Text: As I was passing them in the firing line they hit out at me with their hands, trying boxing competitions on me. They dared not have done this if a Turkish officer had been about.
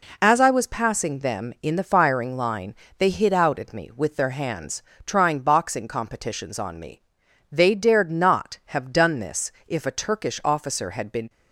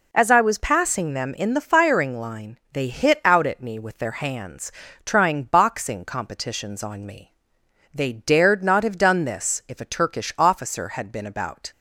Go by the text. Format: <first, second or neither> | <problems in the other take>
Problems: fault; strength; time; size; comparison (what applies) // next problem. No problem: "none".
second | pauses between "line" and "they"; slight; at 2.7 s; 0.22 s long; slight in the second // pauses between "this" and "if"; slight; at 9.4 s; 0.16 s long // stops before "about"; at 11.2 s